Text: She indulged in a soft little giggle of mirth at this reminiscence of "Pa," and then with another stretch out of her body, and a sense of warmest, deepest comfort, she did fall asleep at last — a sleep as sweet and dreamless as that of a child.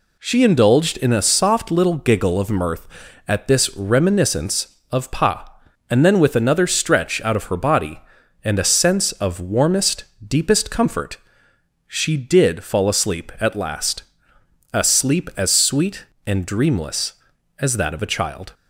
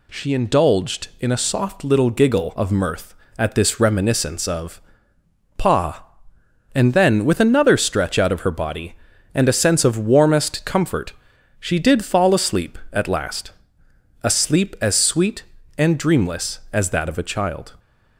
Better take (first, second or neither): first